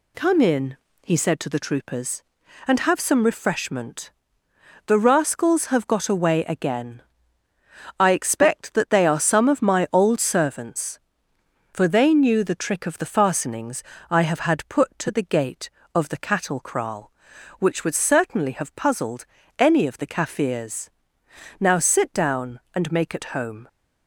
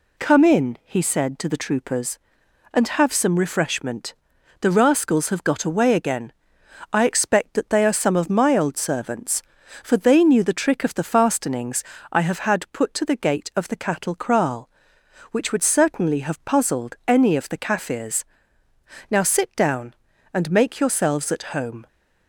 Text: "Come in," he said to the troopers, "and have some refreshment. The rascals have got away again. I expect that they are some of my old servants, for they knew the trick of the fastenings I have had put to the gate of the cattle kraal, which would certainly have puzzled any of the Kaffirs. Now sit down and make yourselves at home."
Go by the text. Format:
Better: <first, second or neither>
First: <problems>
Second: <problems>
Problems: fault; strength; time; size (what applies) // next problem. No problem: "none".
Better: second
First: pauses between "fastenings" and "I"; slight; at 13.8 s; 0.26 s long // pauses between "puzzled" and "any"; slight; at 19.2 s; 0.34 s long // skips "yourselves"; at 23.1 s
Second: pauses between "fastenings" and "I"; slight; at 11.8 s; 0.28 s long